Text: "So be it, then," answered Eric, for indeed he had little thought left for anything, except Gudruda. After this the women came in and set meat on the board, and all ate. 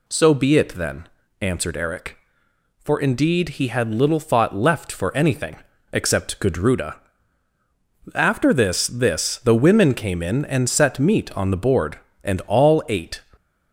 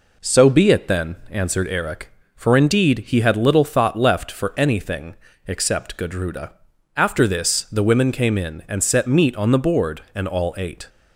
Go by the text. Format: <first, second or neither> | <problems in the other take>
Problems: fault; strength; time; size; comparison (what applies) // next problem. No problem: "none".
second | says "this" twice; at 8.8 s